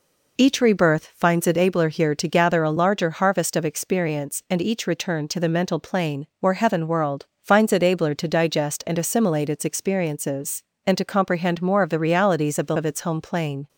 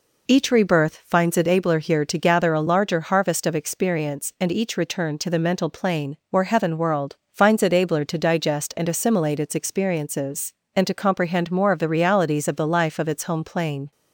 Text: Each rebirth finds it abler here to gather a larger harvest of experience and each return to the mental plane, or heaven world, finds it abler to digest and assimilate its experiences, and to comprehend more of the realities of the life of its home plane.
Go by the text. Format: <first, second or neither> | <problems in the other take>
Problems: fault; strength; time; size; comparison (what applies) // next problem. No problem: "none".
second | skips "life"; at 12.7 s